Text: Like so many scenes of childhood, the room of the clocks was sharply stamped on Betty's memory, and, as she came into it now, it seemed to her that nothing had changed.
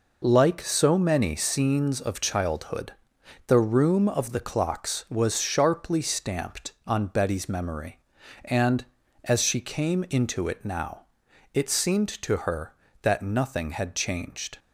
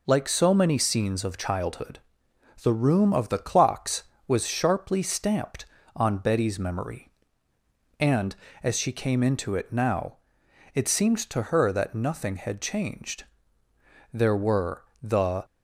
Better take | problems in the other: first | goes on to say "There were the"; from 14.1 s on; 1.3 s long

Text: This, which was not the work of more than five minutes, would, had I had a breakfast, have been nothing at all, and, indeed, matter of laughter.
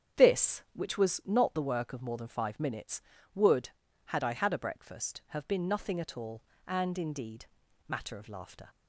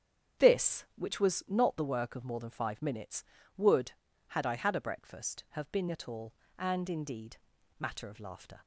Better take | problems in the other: first | starts louder than the rest; strong; until 1.5 s; 8.5 dB; strong in the first // skips "nothing"; at 5.8 s

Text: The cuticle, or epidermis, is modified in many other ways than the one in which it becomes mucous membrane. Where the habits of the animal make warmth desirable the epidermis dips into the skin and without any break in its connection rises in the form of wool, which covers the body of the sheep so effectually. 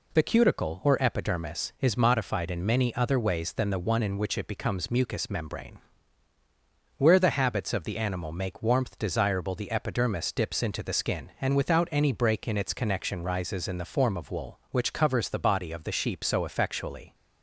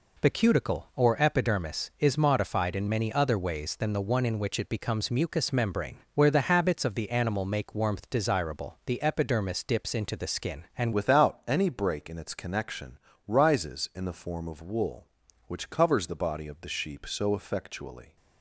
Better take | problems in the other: first | changes voice at "without"; from 10.9 s on; 7.2 s long // pauses between "connection" and "rises"; slight; at 12.9 s; 0.30 s long

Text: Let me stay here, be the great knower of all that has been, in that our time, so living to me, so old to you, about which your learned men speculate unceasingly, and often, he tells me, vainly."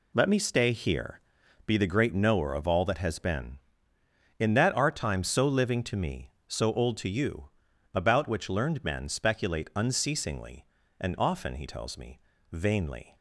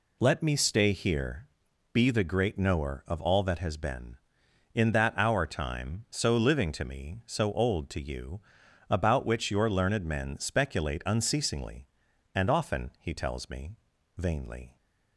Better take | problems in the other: second | skips "your"; at 8.4 s

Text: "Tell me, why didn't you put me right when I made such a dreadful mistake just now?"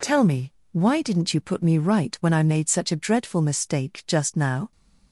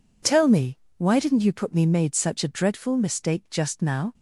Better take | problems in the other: first | skips "right when I"; at 1.8 s

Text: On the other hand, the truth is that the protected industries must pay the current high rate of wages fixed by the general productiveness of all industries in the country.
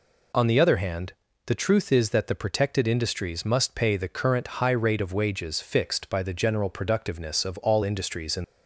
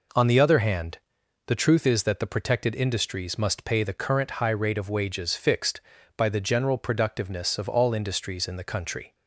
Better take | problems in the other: second | stops before "the country"; at 8.4 s

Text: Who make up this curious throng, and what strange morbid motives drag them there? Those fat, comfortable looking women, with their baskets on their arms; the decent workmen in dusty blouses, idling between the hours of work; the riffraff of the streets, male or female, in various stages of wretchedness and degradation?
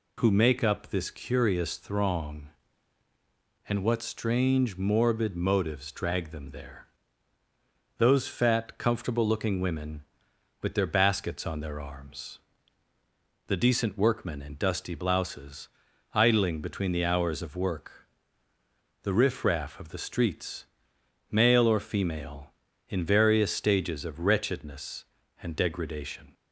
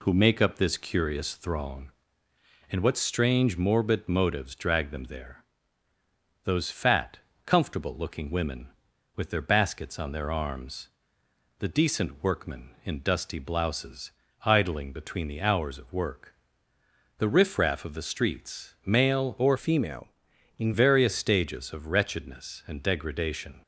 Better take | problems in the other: first | changes voice from "female" to "in"; from 19.5 to 20.7 s; 1.2 s long

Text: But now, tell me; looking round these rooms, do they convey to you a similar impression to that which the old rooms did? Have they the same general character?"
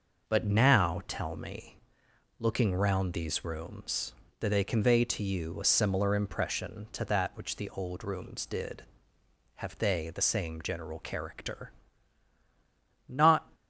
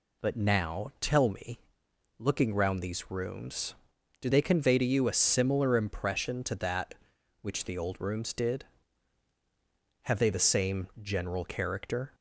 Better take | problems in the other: second | goes on to say "Not"; slight; from 13.0 s on; 0.44 s long

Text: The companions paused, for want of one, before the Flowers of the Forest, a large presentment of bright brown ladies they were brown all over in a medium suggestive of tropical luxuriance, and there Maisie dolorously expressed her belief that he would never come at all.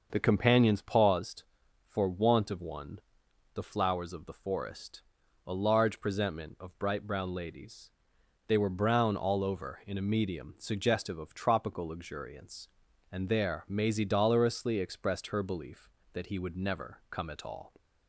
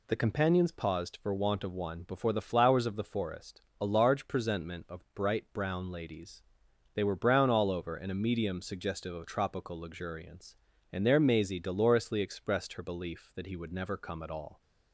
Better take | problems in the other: second | starts louder than the rest; until 1.1 s; 6 dB // skips "before"; at 3.2 s // pauses between "ladies" and "they"; noticeable; at 7.9 s; 0.56 s long; noticeable in the second

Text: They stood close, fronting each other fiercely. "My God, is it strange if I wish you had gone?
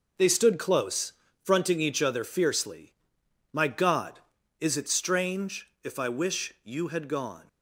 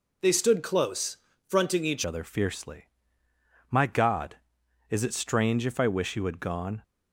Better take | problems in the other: first | changes voice at "other"; from 2.0 s on; 4.8 s long

